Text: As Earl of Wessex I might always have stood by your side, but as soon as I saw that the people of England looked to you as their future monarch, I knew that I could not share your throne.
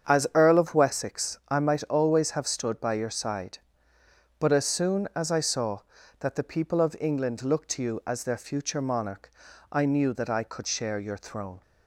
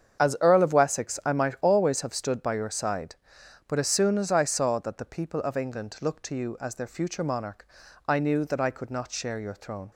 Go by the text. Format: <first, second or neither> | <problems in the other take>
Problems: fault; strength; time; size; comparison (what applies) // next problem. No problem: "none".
second | starts louder than the rest; strong; until 1.1 s; 7.5 dB; strong in the second // skips "not"; at 10.6 s